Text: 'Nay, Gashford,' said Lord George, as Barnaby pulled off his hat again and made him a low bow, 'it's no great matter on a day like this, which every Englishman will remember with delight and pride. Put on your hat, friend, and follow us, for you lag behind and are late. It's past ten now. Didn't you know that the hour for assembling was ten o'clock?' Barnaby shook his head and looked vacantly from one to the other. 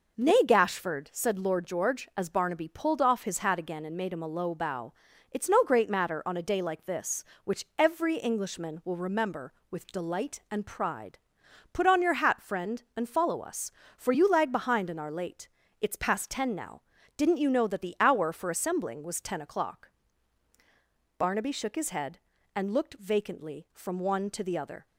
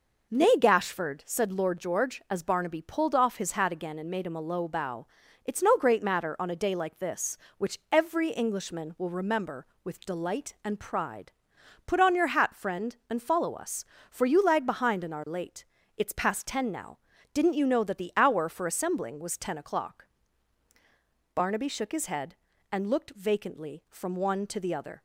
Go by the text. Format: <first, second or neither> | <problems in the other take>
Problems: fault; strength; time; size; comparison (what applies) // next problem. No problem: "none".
neither | none